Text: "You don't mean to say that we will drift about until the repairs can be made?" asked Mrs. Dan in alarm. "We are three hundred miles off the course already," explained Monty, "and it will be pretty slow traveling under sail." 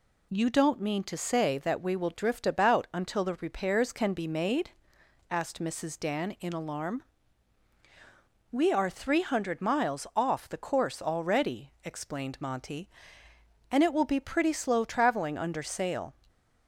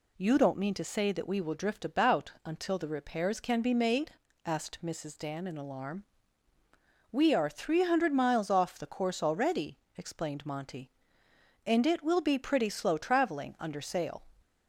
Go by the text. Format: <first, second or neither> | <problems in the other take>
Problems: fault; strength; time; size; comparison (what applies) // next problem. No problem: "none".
neither | none